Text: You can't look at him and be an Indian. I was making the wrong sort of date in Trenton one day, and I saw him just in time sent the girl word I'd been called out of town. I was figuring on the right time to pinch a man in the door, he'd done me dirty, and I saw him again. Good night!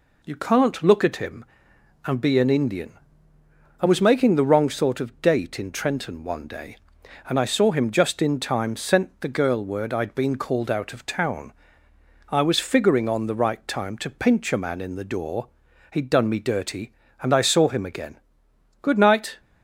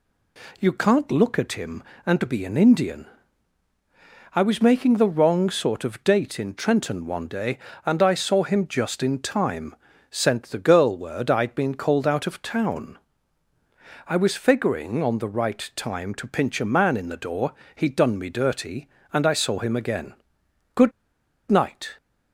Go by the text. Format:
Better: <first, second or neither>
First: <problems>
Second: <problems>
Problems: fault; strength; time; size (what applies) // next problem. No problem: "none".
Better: first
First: none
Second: pauses between "time" and "sent"; slight; at 9.7 s; 0.34 s long // pauses between "Good" and "night"; noticeable; at 20.9 s; 0.58 s long